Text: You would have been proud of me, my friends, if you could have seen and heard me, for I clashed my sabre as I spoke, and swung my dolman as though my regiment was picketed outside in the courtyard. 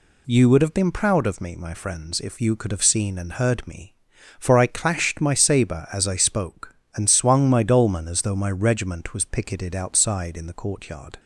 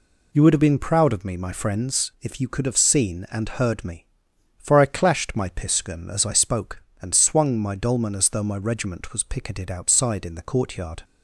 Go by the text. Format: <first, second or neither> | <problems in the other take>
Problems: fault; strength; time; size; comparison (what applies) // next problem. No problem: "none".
first | says "piskun" for "sabre"; at 5.5 s